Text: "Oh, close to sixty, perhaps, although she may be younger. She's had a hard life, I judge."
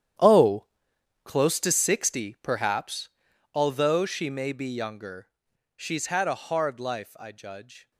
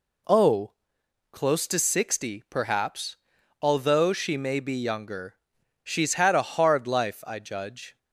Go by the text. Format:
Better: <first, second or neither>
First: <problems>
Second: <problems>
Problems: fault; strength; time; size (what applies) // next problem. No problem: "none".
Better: second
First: gets quieter; strong; throughout; 16 dB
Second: none